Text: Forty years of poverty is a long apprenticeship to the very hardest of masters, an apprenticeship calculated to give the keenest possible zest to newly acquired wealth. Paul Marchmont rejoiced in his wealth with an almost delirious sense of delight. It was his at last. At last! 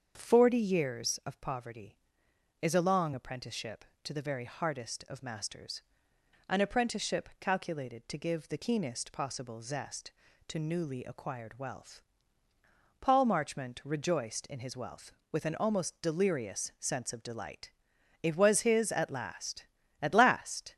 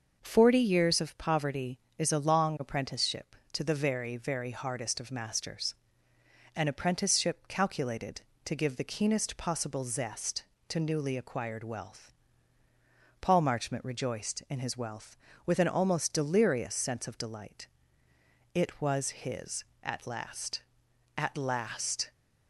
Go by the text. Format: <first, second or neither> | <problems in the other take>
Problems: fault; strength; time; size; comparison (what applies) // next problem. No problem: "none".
first | starts louder than the rest; noticeable; until 1.2 s; 6 dB; strong in the first // says "very" twice; at 4.1 s